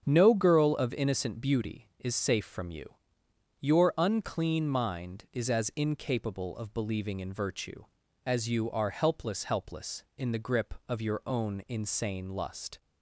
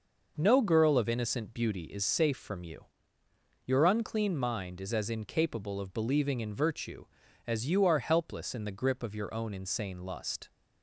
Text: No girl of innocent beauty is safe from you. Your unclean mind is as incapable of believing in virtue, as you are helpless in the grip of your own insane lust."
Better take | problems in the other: second | starts louder than the rest; strong; until 1.0 s; 7.5 dB // says "helpless" twice; at 9.4 s

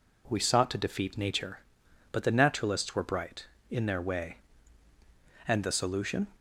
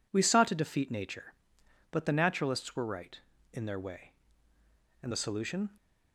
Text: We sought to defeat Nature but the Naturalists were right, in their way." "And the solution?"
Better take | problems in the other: second | says "bright" for "right"; at 3.0 s

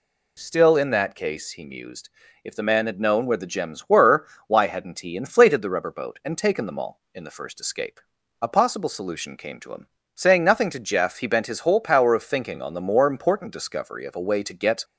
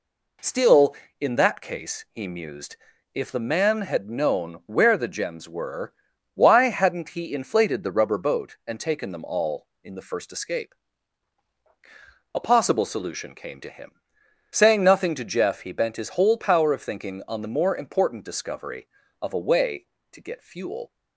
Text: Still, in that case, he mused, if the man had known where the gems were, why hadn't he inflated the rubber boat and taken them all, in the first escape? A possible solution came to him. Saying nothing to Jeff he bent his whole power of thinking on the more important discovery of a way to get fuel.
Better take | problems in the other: second | stops before "fuel"; at 14.8 s

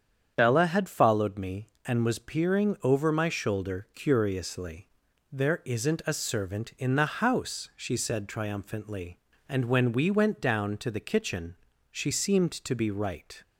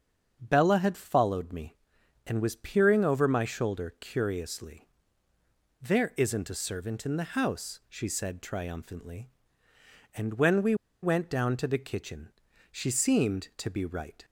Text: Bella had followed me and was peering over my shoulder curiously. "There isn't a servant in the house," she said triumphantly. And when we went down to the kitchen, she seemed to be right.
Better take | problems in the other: first | starts louder than the rest; until 1.4 s; 7 dB; strong in the first // pauses between "we" and "went"; slight; at 10.7 s; 0.28 s long

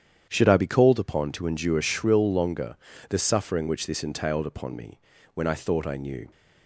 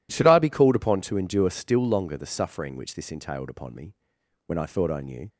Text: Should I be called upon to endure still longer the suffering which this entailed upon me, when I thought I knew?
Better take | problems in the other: second | starts louder than the rest; strong; until 1.3 s; 9 dB // says "shrill" for "still"; at 1.7 s // pauses between "longer" and "the"; slight; at 2.7 s; 0.32 s long

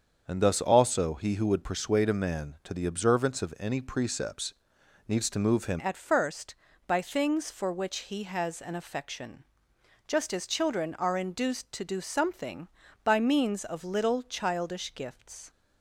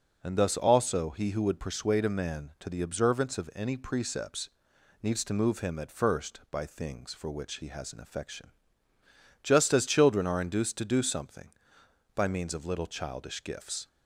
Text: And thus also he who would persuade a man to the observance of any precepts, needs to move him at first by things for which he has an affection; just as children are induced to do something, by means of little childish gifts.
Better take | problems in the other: second | starts louder than the rest; until 1.2 s; 7 dB // changes voice at "at"; from 5.7 s on; 9.7 s long

